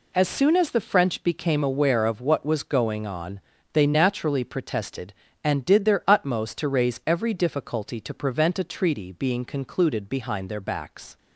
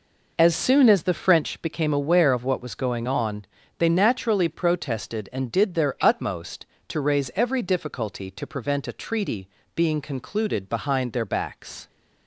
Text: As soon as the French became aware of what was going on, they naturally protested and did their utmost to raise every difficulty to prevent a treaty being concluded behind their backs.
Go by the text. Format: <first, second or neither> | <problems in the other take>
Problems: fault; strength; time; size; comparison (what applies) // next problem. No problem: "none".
first | starts louder than the rest; noticeable; until 1.7 s; 5 dB // pauses between "treaty" and "being"; slight; at 9.4 s; 0.26 s long